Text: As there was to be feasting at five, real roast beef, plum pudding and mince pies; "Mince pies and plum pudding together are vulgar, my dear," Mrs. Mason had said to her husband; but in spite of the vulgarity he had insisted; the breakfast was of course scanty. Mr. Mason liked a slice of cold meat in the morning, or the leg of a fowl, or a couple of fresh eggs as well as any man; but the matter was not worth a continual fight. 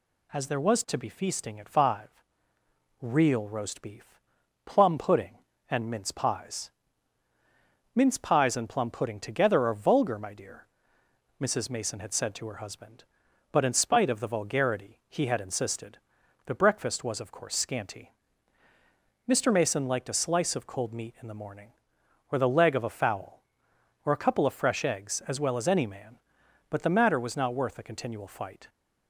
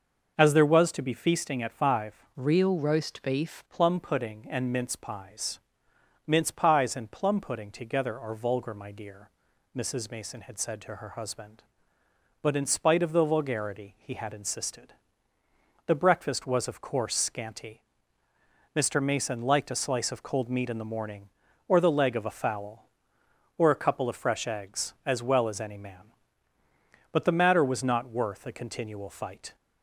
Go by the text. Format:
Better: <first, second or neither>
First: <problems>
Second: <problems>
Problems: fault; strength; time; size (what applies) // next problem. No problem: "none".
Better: first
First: none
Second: starts louder than the rest; until 1.3 s; 6 dB // changes voice from "real" to "beef"; from 2.3 to 3.6 s; 1.3 s long